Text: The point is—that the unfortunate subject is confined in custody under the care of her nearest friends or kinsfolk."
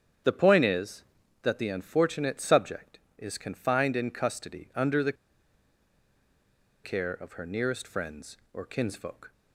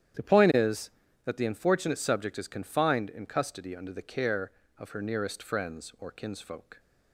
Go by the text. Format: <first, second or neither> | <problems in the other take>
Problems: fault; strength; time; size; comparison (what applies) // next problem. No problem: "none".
second | starts louder than the rest; strong; until 1.6 s; 8.5 dB; strong in the second // pauses between "the" and "care"; strong; at 5.1 s; 1.7 s long